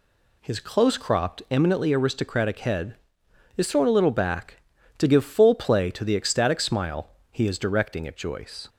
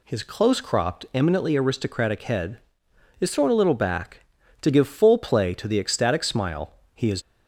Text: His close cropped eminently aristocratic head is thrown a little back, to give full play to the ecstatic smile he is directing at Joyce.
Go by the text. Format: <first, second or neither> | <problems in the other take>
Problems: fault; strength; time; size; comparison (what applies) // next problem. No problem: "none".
first | pauses between "smile" and "he"; slight; at 6.7 s; 0.22 s long; slight in the first // stops before "directing at Joyce"; at 7.2 s